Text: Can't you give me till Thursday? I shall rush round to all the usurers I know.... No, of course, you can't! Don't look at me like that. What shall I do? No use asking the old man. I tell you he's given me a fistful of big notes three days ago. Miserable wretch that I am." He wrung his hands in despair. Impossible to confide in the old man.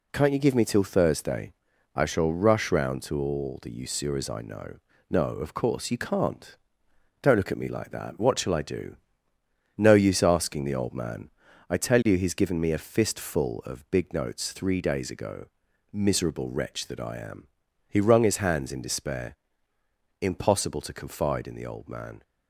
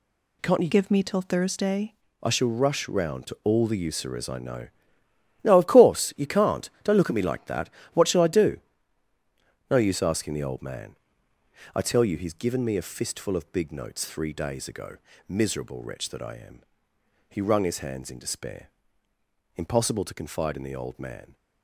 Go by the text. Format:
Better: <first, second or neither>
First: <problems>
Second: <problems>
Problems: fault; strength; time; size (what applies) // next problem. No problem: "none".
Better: first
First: none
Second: changes voice from "give" to "Thursday"; from 0.6 to 1.9 s; 1.3 s long